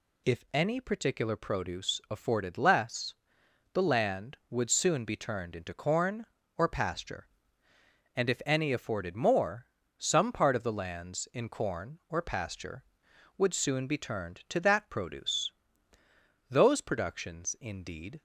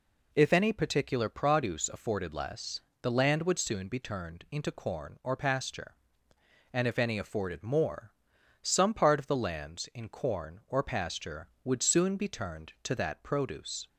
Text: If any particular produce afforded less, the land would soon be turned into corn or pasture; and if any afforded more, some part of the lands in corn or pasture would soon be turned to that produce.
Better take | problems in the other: second | goes on to say "Those productions indeed"; strong; from 16.4 s on; 1.7 s long

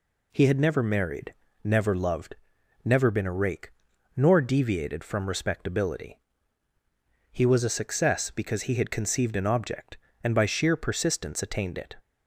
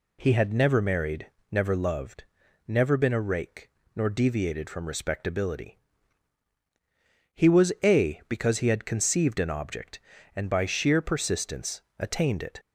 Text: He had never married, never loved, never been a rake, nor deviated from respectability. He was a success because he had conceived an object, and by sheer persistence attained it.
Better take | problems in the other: first | skips "success"; at 8.2 s // pauses between "persistence" and "attained"; slight; at 11.7 s; 0.18 s long

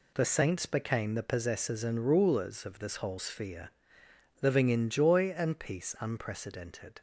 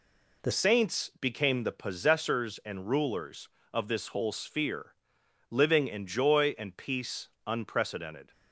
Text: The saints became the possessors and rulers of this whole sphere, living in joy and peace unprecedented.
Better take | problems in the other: first | changes voice at "saints"; from 0.5 s on; 7.8 s long // pauses between "peace" and "unprecedented"; slight; at 7.2 s; 0.16 s long

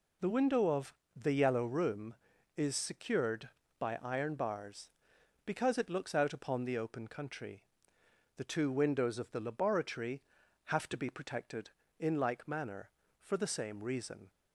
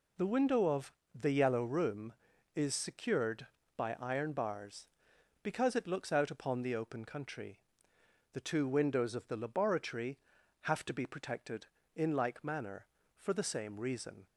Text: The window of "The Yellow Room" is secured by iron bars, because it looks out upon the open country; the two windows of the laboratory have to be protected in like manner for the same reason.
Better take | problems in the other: neither | pauses between "of" and "The"; slight; the same in both

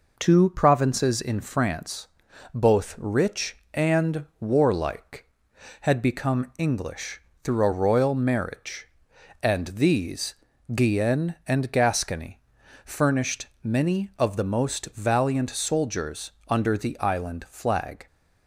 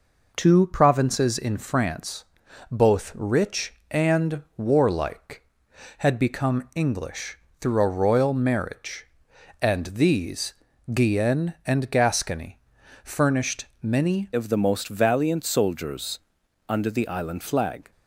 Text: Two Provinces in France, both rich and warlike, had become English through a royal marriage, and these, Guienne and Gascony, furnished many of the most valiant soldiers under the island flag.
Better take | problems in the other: first | pauses between "English" and "through"; slight; at 7.3 s; 0.22 s long; slight in the first // pauses between "furnished" and "many"; slight; at 13.6 s; 0.16 s long; slight in the first // changes voice at "of"; from 14.3 s on; 3.6 s long // pauses between "soldiers" and "under"; noticeable; at 16.1 s; 0.48 s long; slight in the first

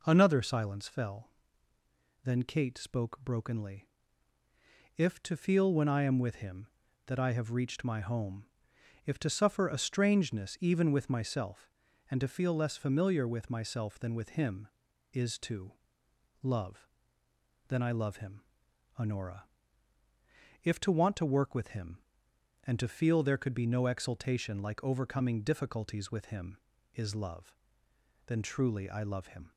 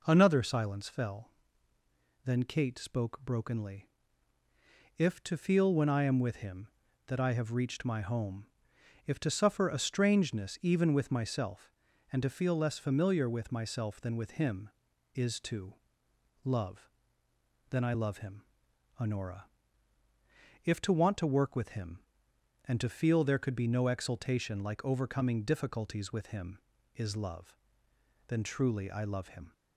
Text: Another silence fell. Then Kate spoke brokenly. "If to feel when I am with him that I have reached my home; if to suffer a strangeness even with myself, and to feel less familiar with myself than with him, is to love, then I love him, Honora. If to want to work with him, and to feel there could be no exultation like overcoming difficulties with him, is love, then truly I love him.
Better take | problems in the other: neither | pauses between "to" and "love"; noticeable; the same in both

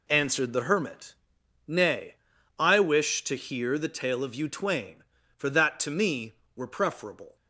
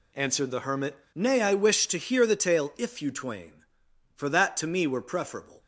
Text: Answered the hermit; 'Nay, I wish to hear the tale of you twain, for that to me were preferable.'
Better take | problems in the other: first | says "if" for "of"; at 2.7 s

